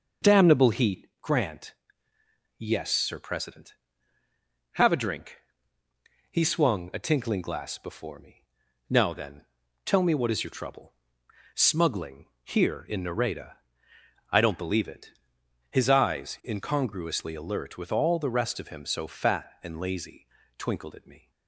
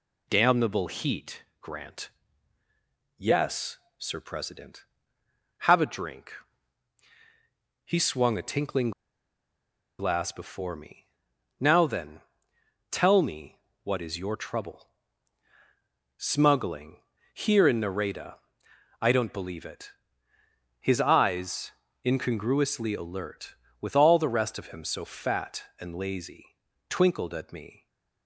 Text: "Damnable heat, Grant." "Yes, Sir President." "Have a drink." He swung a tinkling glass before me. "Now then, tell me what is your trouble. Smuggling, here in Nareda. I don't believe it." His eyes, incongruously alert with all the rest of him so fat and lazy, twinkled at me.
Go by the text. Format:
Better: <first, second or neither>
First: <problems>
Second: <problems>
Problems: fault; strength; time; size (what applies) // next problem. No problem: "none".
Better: first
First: none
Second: pauses between "tinkling" and "glass"; at 8.9 s; 1.0 s long // pauses between "me" and "what"; slight; at 13.5 s; 0.24 s long